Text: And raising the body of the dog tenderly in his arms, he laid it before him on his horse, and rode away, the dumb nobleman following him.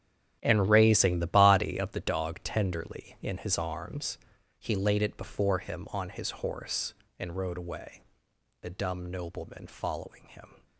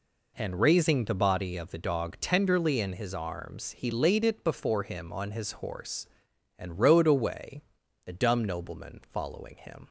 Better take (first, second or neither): second